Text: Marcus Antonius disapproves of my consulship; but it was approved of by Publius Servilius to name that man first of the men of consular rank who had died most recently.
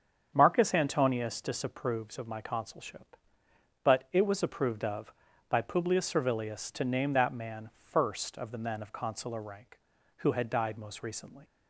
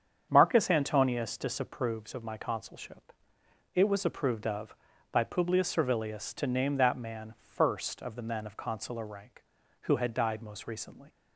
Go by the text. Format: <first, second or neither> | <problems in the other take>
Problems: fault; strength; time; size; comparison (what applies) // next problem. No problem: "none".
first | starts louder than the rest; strong; until 1.3 s; 8 dB; strong in the first // skips "but"; at 3.4 s